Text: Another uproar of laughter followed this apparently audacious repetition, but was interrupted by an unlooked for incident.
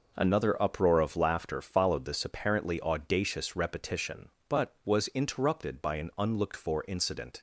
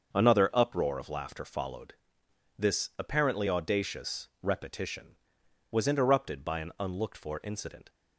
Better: first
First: none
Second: starts louder than the rest; until 1.1 s; 6.5 dB // pauses between "followed" and "this"; noticeable; at 1.9 s; 0.64 s long // skips "but"; at 5.4 s

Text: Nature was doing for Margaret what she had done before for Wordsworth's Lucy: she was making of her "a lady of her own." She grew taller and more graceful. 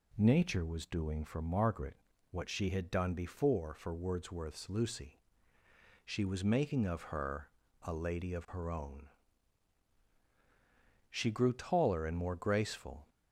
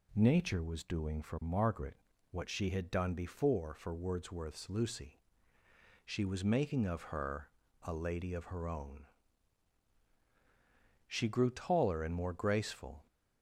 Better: neither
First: pauses between "Margaret" and "what"; slight; at 1.9 s; 0.34 s long // pauses between "her" and "a"; slight; at 7.4 s; 0.32 s long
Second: pauses between "Margaret" and "what"; slight; at 1.9 s; 0.34 s long // pauses between "her" and "a"; slight; at 7.4 s; 0.32 s long

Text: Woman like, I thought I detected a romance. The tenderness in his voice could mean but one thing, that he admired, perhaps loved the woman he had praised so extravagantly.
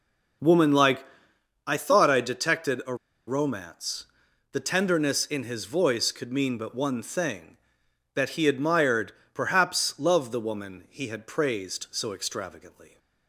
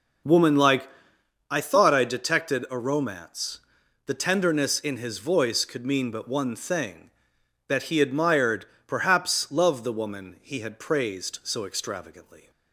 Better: second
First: pauses between "a" and "romance"; slight; at 2.9 s; 0.32 s long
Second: none

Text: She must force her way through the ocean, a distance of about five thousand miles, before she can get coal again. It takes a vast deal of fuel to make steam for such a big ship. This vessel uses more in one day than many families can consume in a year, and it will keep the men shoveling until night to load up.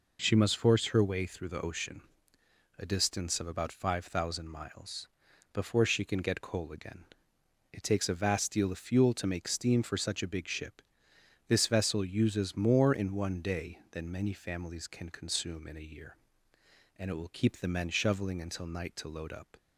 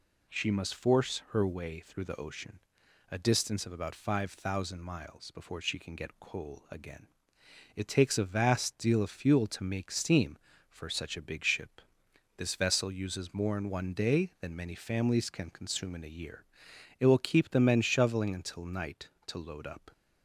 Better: first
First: none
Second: skips "and"; at 16.7 s

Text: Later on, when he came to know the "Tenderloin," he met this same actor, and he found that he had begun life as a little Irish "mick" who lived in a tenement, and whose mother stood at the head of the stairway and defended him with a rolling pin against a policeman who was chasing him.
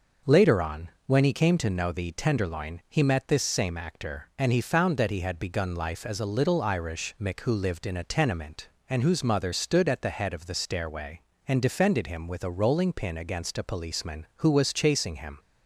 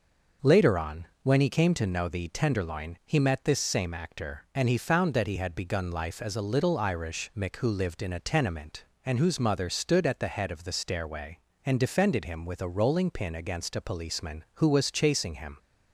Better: neither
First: none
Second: none

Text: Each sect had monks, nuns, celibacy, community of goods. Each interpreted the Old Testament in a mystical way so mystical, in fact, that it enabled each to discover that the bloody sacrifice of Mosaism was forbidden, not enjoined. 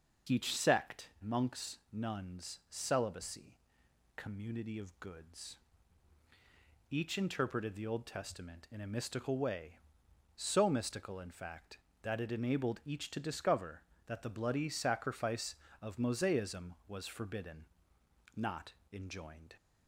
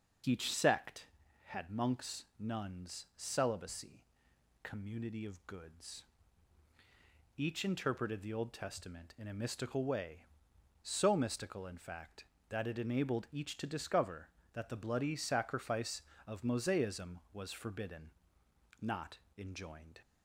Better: second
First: starts louder than the rest; noticeable; until 1.4 s; 6 dB // skips "had"; at 1.1 s // pauses between "not" and "enjoined"; slight; at 18.7 s; 0.18 s long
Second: pauses between "not" and "enjoined"; slight; at 19.1 s; 0.18 s long

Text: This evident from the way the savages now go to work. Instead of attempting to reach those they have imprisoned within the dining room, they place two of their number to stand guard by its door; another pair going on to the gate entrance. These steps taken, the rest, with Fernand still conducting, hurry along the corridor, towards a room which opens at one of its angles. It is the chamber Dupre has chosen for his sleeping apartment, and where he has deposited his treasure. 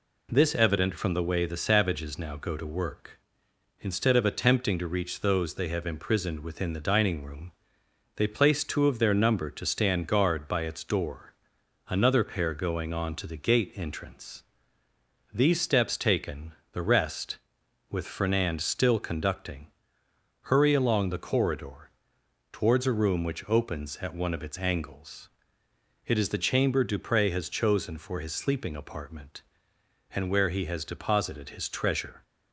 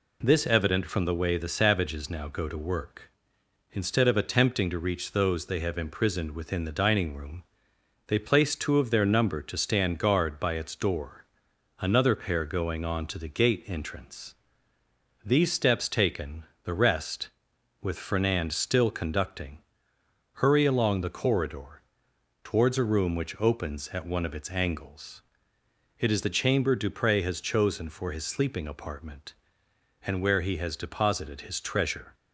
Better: neither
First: none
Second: none

